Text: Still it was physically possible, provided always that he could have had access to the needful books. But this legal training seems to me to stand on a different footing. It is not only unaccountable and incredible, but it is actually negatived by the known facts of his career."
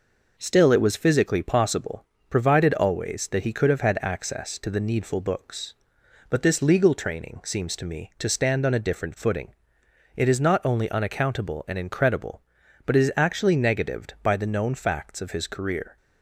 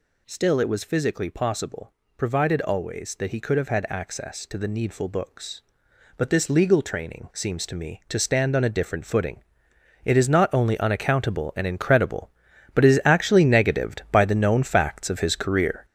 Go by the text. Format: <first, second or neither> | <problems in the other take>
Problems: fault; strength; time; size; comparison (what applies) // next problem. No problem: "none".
first | gets louder; strong; throughout; 7.5 dB